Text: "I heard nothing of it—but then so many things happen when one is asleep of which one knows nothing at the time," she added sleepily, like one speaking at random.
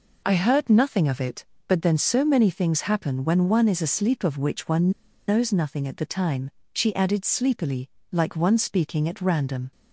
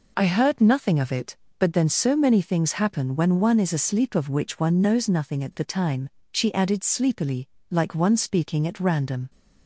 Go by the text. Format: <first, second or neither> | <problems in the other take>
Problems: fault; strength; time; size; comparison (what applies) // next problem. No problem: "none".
second | pauses between "one" and "knows"; at 4.9 s; 0.38 s long